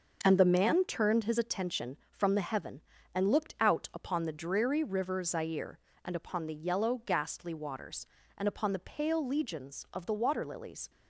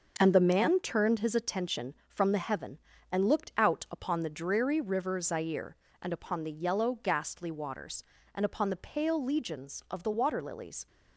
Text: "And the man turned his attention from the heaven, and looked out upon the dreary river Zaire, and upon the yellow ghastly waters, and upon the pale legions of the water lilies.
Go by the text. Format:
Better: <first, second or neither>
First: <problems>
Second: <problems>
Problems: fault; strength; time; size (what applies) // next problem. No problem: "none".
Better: neither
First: starts louder than the rest; until 1.2 s; 6 dB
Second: starts louder than the rest; until 1.1 s; 6 dB